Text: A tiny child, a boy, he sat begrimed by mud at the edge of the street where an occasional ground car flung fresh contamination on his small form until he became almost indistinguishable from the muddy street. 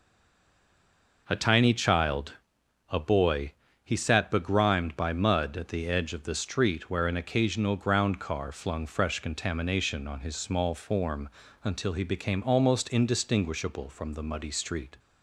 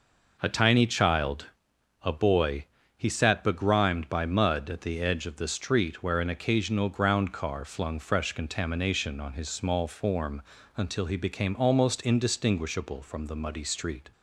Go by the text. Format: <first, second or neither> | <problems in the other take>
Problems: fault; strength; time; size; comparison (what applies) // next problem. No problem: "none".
second | stays silent before the first word; noticeable; until 1.2 s; 1.2 s long // pauses between "form" and "until"; slight; at 11.2 s; 0.34 s long; slight in the second